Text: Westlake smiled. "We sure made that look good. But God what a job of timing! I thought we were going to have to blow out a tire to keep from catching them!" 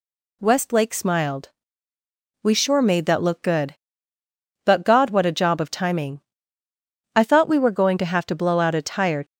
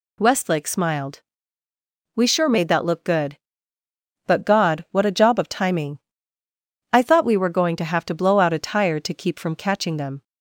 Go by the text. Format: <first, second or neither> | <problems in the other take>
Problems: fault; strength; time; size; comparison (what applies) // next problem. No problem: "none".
second | stops before "to keep from catching them"; at 9.2 s